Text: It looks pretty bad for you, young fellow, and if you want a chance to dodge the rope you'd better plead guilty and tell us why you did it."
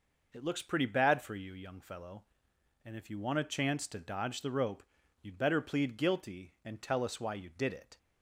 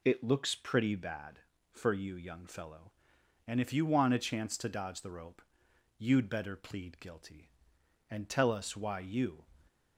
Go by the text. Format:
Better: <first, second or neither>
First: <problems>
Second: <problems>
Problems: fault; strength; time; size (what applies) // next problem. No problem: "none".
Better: first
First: pauses between "rope" and "you'd"; slight; at 4.8 s; 0.36 s long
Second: pauses between "rope" and "you'd"; noticeable; at 5.4 s; 0.56 s long // stops before "did it"; at 9.6 s